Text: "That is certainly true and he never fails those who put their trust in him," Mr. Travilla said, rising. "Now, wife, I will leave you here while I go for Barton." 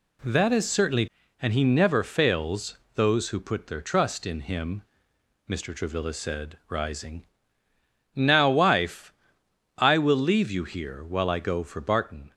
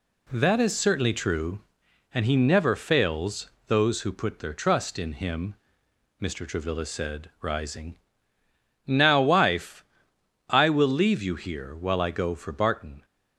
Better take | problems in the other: second | skips "true"; at 1.2 s // pauses between "fails" and "those"; slight; at 2.7 s; 0.18 s long; slight in the second

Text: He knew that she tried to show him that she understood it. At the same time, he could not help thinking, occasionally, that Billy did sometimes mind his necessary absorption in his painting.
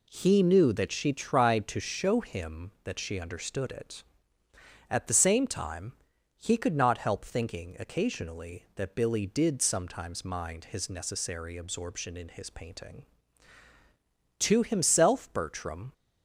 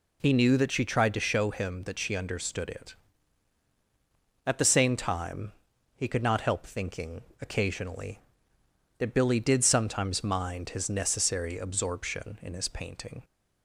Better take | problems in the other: second | goes on to say "To himself Bertram"; from 14.3 s on; 1.5 s long

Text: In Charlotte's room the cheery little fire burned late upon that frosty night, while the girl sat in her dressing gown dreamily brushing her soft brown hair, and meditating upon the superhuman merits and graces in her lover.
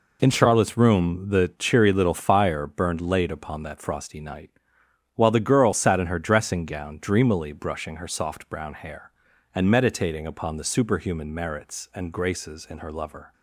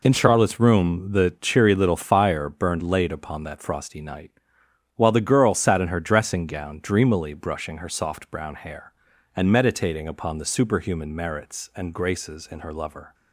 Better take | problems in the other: neither | none

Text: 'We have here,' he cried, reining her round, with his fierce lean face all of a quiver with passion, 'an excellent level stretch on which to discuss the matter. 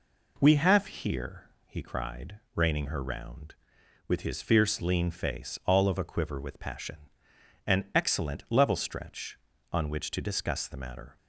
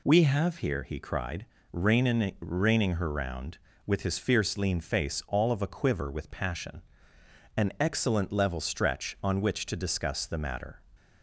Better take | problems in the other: first | says "reining" twice; at 2.4 s

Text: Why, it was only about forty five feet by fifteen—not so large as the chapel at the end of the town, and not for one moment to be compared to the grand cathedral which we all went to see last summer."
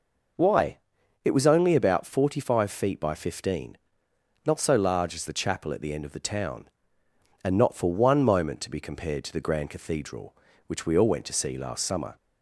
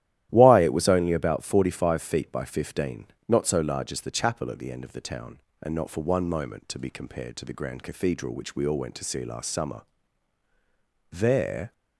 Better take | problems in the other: first | starts louder than the rest; strong; until 1.3 s; 13 dB // goes on to say "There"; noticeable; from 11.1 s on; 0.62 s long

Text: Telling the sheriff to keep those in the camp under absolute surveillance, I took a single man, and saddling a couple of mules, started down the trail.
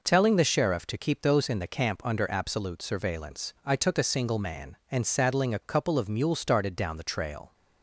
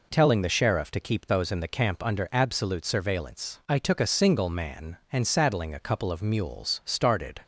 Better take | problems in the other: first | stops before "down the trail"; at 7.4 s

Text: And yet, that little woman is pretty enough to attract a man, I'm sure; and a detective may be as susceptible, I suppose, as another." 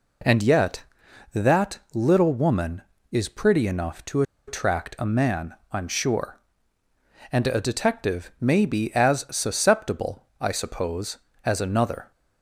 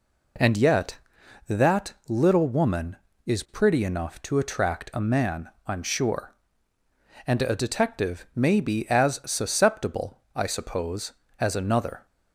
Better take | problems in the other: second | pauses between "to" and "attract"; slight; at 4.2 s; 0.25 s long

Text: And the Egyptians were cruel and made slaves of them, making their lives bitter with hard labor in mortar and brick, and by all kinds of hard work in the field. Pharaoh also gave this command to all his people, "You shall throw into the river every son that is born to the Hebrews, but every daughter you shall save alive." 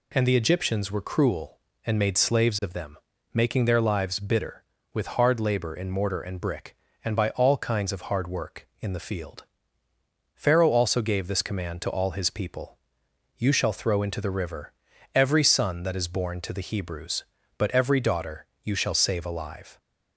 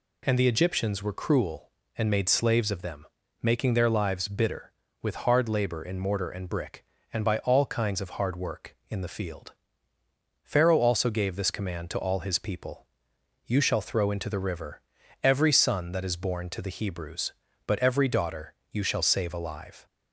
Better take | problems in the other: neither | pauses between "river" and "every"; the same in both // pauses between "daughter" and "you"; slight; the same in both

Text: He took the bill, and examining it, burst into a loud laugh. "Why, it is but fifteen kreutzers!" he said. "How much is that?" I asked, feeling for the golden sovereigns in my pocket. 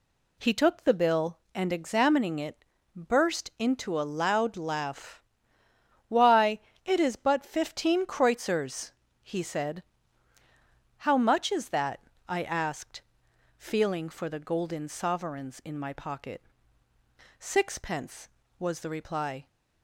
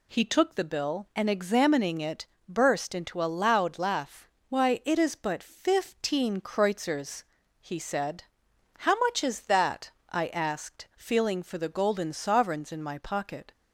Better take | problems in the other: second | goes on to say "Sixpence was the reply"; strong; from 17.3 s on; 2.0 s long

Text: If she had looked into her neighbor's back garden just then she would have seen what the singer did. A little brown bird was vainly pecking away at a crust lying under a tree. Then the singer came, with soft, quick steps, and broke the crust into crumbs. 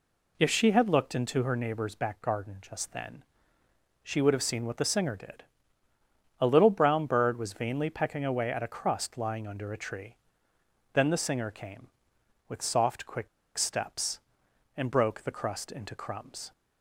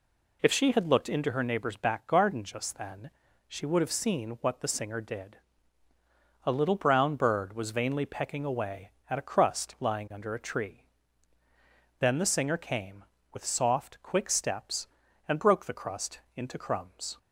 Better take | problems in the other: second | pauses between "then" and "she"; noticeable; at 3.2 s; 0.80 s long; also in the second // pauses between "quick" and "steps"; slight; at 13.2 s; 0.29 s long

